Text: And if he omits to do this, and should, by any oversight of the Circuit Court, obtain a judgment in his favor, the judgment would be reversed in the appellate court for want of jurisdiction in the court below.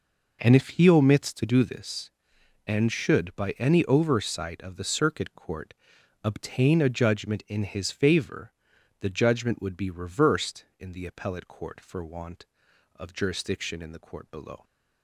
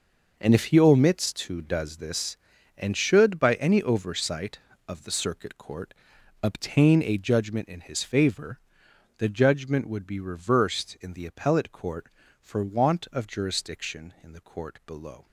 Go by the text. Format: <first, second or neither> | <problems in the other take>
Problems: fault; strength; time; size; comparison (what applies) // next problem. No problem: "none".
first | says "does" for "do"; at 1.6 s